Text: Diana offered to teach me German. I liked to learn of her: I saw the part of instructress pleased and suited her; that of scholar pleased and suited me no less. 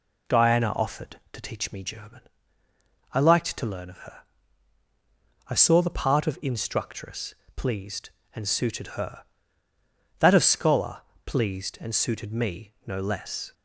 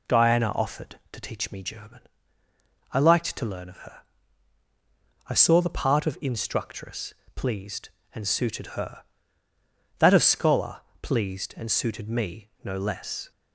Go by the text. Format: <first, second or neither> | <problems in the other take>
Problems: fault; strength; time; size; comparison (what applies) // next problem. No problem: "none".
neither | pauses between "instructress" and "pleased"; slight; the same in both // pauses between "scholar" and "pleased"; slight; the same in both